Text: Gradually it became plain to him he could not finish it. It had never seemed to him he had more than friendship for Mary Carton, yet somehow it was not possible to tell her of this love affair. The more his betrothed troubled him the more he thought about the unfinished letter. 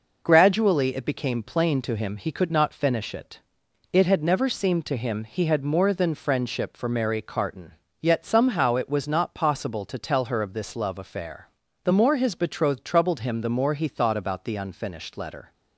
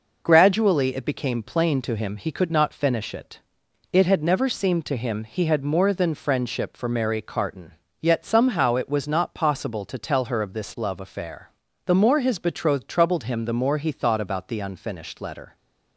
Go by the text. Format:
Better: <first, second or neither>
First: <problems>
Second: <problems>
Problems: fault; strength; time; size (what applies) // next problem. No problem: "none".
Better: neither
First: none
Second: none